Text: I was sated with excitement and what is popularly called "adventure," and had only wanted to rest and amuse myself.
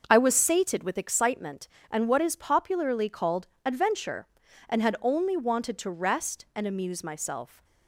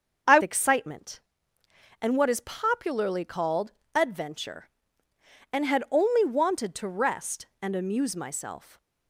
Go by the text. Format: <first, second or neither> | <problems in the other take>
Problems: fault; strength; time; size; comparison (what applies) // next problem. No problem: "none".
first | starts louder than the rest; until 2.1 s; 6.5 dB; also in the first // skips "was sated with"; at 0.4 s // pauses between "called" and "adventure"; slight; at 3.7 s; 0.24 s long; slight in the first // stays silent after the last word; slight; from 8.5 s on; 0.5 s long